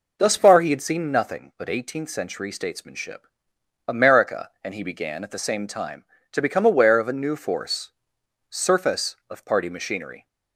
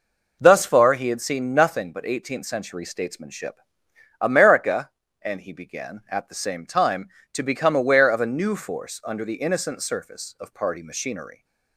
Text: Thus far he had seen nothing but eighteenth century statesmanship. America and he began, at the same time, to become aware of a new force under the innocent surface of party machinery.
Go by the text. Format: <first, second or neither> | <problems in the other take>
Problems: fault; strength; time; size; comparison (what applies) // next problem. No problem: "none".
second | skips "under the innocent"; at 8.2 s